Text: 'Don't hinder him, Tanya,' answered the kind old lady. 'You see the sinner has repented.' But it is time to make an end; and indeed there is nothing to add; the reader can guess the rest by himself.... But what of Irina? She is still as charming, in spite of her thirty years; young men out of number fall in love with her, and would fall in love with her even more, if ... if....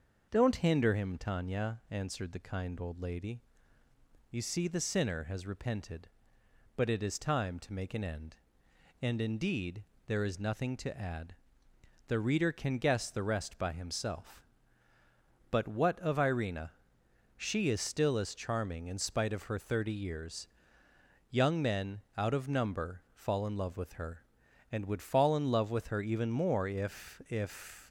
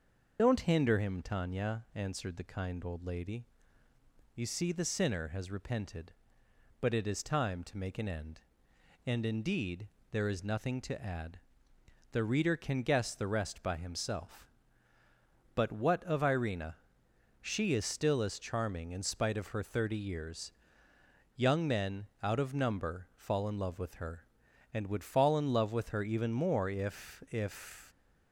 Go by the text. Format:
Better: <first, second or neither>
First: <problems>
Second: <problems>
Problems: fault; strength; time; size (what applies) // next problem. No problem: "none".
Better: first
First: starts louder than the rest; until 1.3 s; 6 dB // pauses between "indeed" and "there"; slight; at 9.8 s; 0.22 s long // pauses between "men" and "out"; slight; at 22.0 s; 0.16 s long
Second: loses the start of "Don't"; at 0.3 s; 50 ms // starts louder than the rest; until 1.4 s; 6 dB // pauses between "indeed" and "there"; slight; at 9.8 s; 0.22 s long // pauses between "men" and "out"; slight; at 22.0 s; 0.16 s long